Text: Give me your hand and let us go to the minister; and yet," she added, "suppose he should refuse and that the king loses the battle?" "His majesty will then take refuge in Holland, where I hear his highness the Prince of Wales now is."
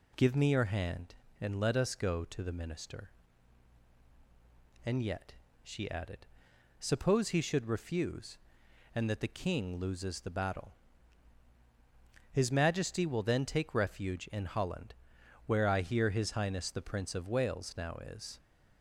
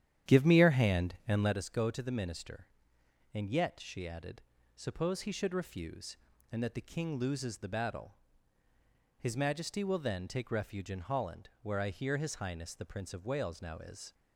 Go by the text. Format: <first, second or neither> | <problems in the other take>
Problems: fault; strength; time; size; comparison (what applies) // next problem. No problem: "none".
first | starts louder than the rest; strong; until 1.6 s; 10.5 dB